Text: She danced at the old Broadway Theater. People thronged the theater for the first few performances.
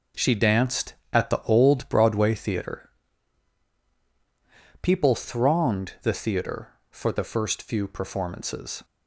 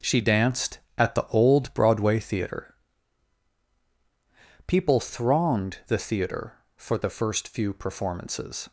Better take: neither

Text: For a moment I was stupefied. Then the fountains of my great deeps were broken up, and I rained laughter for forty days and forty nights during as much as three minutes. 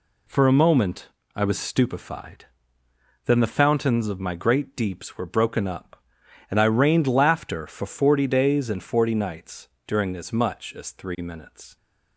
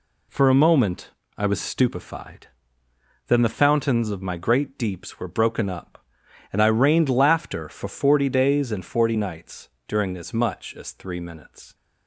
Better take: neither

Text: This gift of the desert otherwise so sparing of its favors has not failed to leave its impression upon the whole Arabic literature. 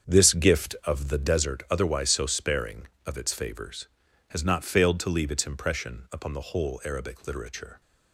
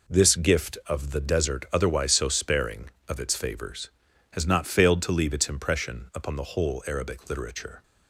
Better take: second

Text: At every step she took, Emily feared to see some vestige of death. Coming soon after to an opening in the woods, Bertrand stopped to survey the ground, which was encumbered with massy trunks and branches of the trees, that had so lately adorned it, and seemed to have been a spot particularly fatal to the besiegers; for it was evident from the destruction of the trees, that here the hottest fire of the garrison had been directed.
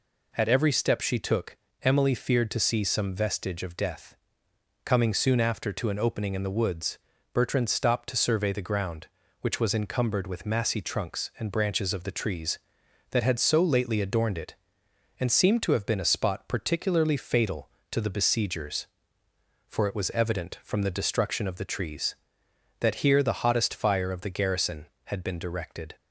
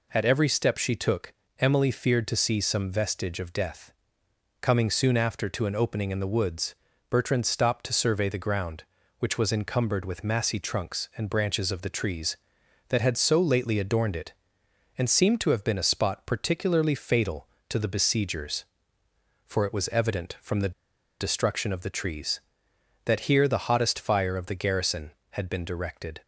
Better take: first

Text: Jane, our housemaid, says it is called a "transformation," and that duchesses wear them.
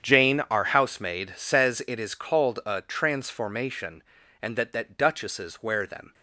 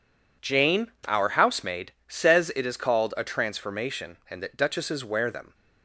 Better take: second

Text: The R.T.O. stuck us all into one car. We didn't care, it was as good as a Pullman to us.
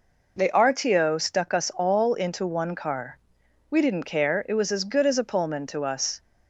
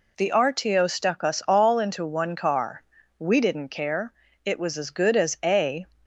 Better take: first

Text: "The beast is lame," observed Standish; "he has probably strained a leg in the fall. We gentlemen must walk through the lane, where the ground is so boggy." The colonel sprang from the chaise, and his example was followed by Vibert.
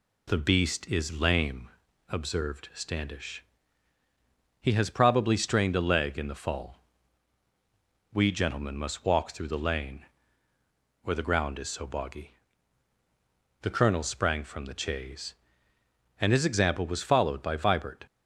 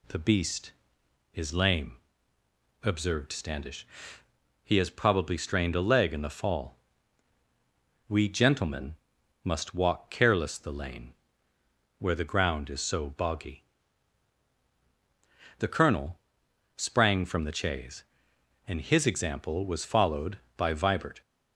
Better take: first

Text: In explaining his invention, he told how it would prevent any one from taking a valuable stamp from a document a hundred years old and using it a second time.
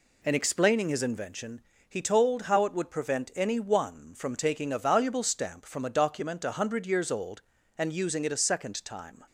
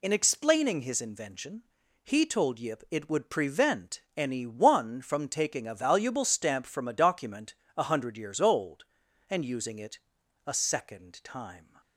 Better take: first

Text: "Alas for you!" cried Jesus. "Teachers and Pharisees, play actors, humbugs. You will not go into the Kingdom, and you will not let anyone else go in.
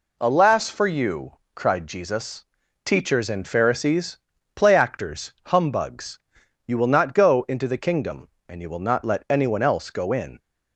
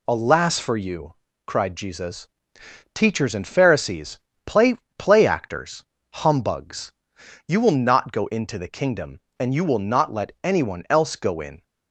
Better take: first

